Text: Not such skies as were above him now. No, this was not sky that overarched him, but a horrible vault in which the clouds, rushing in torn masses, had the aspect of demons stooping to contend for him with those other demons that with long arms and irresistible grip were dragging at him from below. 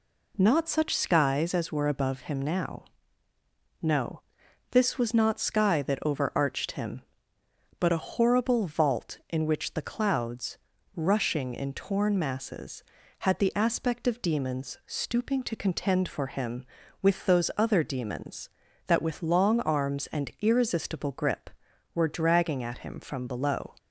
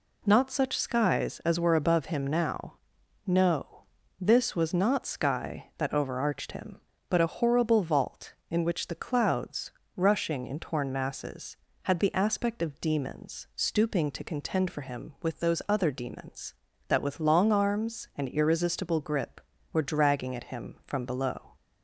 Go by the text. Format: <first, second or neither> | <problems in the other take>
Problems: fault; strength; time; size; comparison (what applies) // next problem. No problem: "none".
neither | none